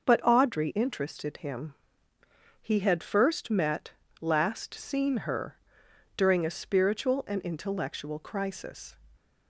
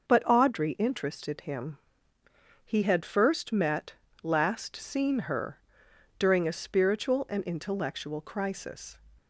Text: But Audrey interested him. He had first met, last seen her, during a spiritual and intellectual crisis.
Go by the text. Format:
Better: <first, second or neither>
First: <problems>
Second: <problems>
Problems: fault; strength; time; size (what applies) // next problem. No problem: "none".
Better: neither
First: none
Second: none